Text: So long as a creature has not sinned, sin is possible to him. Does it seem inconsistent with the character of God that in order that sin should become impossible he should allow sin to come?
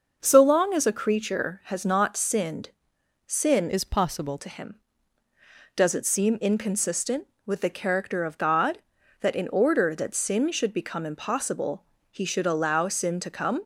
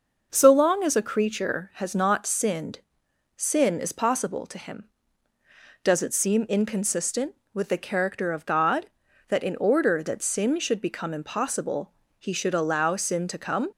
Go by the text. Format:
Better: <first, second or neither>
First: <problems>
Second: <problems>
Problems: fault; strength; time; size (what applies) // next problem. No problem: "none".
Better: second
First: changes voice from "is" to "possible"; from 3.6 to 4.3 s; 0.7 s long // pauses between "impossible" and "he"; slight; at 11.8 s; 0.28 s long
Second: pauses between "impossible" and "he"; slight; at 11.9 s; 0.28 s long